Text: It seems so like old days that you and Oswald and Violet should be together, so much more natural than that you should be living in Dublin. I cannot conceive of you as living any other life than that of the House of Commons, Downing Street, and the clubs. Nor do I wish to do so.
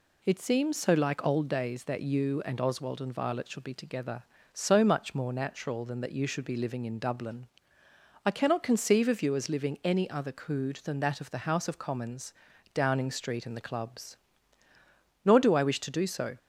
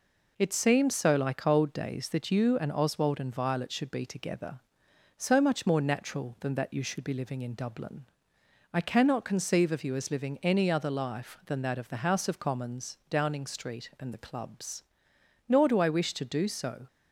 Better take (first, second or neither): second